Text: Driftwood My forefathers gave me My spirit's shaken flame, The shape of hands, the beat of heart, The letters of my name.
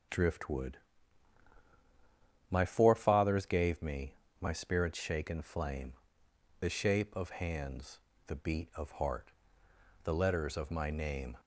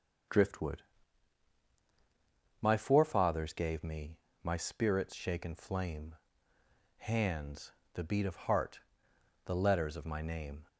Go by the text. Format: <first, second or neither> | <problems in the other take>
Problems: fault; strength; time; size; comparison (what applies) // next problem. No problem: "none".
first | starts louder than the rest; until 3.0 s; 6.5 dB // pauses between "Driftwood" and "My"; strong; at 0.8 s; 1.7 s long; strong in the first // pauses between "me" and "My"; slight; at 4.1 s; 0.24 s long; slight in the first // skips "The shape of"; at 6.5 s